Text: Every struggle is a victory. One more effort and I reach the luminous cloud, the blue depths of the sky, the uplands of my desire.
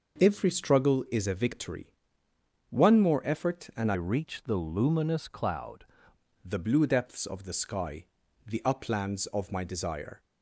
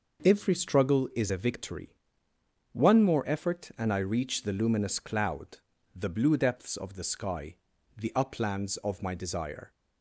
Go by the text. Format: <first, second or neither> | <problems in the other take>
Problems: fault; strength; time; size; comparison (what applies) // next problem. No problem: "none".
second | changes voice from "reach" to "cloud"; from 3.9 to 5.8 s; 1.9 s long